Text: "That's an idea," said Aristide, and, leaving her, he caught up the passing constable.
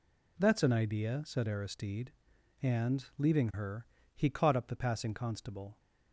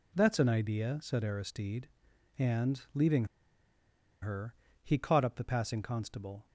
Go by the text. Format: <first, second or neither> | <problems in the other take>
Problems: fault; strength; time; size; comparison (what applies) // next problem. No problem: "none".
first | pauses between "leaving" and "her"; noticeable; at 3.2 s; 0.96 s long